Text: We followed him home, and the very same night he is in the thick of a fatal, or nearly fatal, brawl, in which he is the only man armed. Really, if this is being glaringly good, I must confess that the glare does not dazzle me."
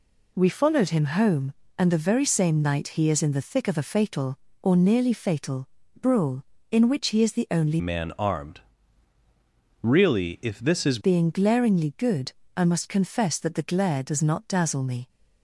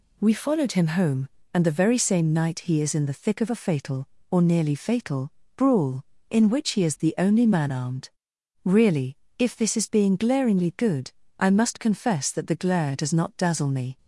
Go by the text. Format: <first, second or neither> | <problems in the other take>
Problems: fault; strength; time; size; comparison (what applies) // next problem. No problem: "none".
second | changes voice from "man" to "is"; from 7.7 to 10.9 s; 3.2 s long